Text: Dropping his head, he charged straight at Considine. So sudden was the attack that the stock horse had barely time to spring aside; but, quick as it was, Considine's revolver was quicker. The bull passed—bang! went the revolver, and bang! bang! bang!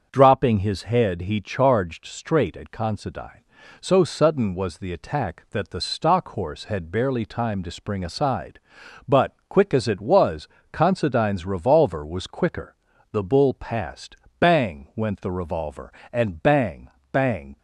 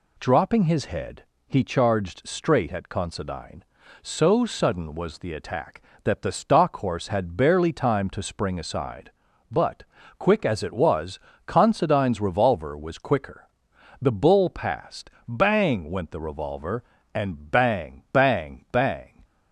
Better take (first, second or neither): second